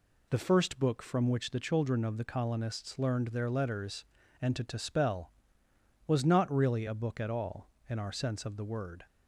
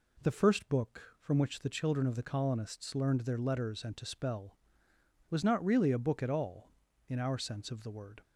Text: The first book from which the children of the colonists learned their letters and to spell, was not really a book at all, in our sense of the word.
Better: second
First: says "to" twice; at 4.6 s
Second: none

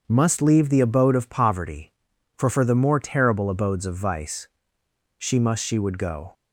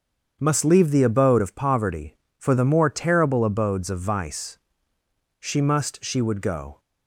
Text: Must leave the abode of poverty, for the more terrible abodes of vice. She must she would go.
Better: second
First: starts louder than the rest; until 1.0 s; 6.5 dB // says "for" twice; at 2.5 s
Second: starts louder than the rest; strong; until 1.4 s; 7 dB

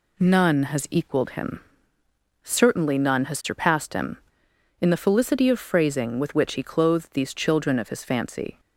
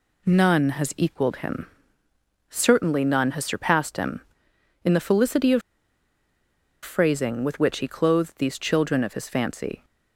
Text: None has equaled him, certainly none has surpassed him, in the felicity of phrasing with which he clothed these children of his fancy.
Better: first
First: none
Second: pauses between "of" and "phrasing"; at 5.6 s; 1.2 s long

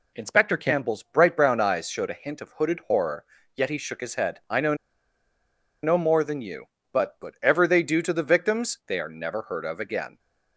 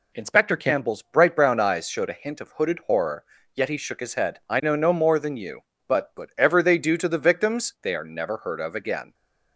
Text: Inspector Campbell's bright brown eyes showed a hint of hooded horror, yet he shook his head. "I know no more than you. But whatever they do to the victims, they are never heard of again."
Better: second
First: pauses between "know" and "no"; at 4.7 s; 1.0 s long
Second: none

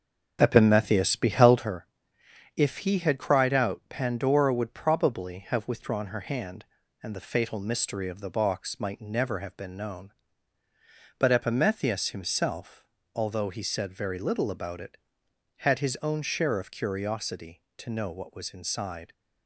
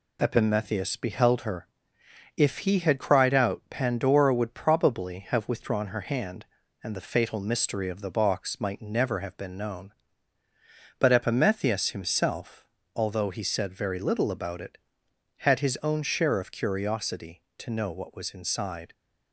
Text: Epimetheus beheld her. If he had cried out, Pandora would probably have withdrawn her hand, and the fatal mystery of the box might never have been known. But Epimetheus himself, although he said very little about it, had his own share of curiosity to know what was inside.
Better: second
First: starts louder than the rest; until 1.7 s; 6.5 dB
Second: none

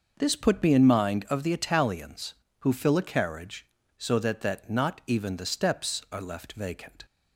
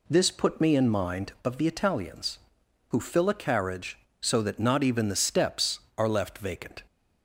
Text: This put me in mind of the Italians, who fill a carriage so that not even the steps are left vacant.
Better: second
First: says "that" twice; at 4.4 s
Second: none

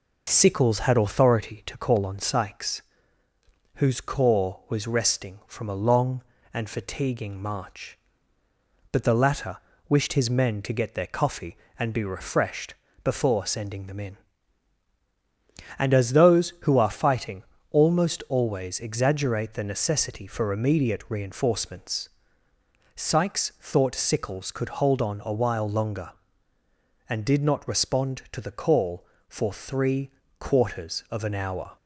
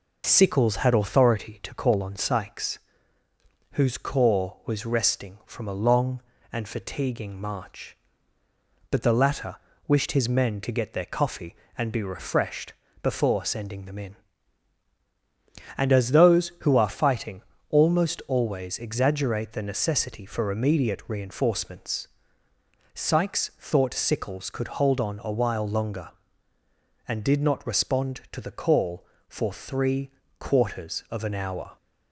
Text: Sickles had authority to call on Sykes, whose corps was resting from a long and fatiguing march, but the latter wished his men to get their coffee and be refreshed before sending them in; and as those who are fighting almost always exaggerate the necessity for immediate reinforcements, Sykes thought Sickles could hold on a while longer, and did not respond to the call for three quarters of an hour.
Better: neither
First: pauses between "latter" and "wished"; slight; at 9.5 s; 0.30 s long // pauses between "refreshed" and "before"; slight; at 12.7 s; 0.30 s long // pauses between "fighting" and "almost"; slight; at 17.4 s; 0.26 s long // pauses between "three" and "quarters"; slight; at 30.1 s; 0.28 s long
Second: pauses between "latter" and "wished"; slight; at 9.5 s; 0.30 s long // pauses between "refreshed" and "before"; slight; at 12.7 s; 0.30 s long // pauses between "fighting" and "almost"; slight; at 17.4 s; 0.26 s long // pauses between "three" and "quarters"; slight; at 30.1 s; 0.28 s long

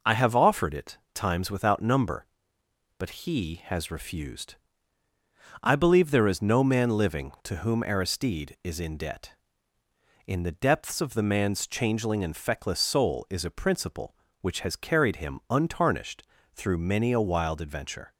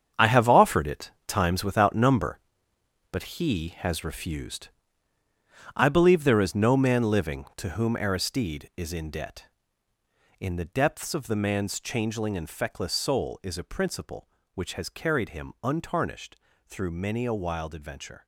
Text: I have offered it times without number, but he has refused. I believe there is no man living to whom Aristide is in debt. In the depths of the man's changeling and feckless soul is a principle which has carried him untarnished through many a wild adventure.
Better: first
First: pauses between "it" and "times"; slight; at 0.9 s; 0.16 s long // pauses between "untarnished" and "through"; slight; at 16.2 s; 0.32 s long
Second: gets quieter; strong; throughout; 11 dB // pauses between "it" and "times"; slight; at 1.0 s; 0.16 s long // pauses between "untarnished" and "through"; slight; at 16.3 s; 0.32 s long

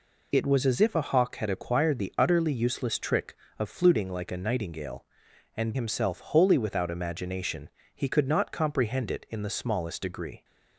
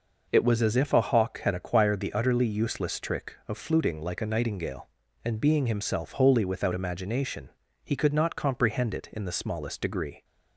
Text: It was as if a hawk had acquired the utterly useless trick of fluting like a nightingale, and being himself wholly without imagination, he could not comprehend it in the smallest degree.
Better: second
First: skips "being"; at 5.7 s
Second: none

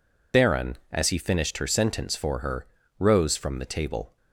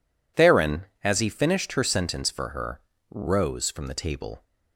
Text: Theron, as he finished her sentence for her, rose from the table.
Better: second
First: loses the start of "Theron"; at 0.3 s; 55 ms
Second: none

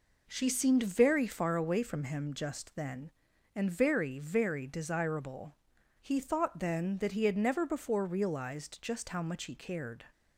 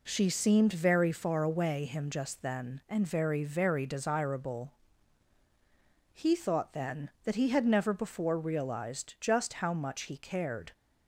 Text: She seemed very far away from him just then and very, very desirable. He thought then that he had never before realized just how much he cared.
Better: first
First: none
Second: skips "from"; at 1.8 s

